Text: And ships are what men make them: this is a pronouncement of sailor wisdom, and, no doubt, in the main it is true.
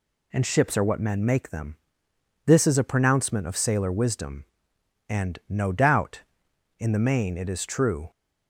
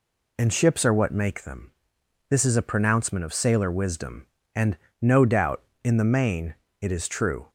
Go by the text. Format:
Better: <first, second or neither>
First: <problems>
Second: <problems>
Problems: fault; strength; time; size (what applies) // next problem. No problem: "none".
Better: first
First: none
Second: skips "men"; at 1.1 s // pauses between "main" and "it"; slight; at 6.5 s; 0.26 s long